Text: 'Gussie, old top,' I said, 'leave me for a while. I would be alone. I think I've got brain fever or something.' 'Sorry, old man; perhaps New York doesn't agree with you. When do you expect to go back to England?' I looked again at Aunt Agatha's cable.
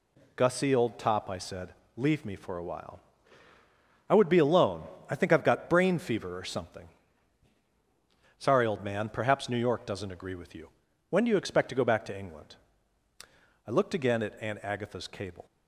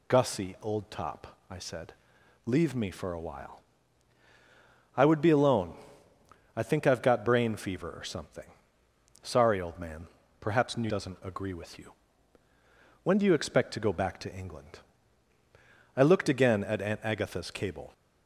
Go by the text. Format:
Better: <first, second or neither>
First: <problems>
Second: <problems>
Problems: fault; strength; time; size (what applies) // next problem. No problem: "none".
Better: first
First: none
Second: skips "York"; at 10.8 s